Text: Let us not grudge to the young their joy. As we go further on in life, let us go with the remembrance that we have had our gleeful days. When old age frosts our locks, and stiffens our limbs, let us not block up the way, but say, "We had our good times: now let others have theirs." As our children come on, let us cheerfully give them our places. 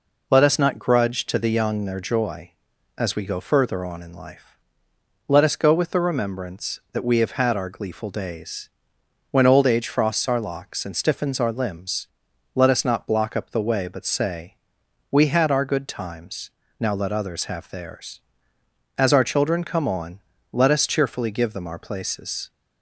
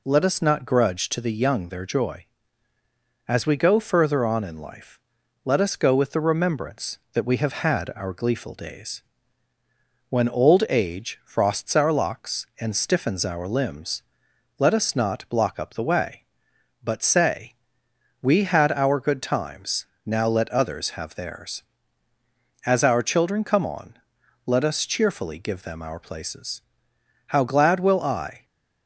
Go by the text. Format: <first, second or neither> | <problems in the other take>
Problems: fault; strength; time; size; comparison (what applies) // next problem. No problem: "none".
first | goes on to say "How glad will I"; noticeable; from 27.2 s on; 1.1 s long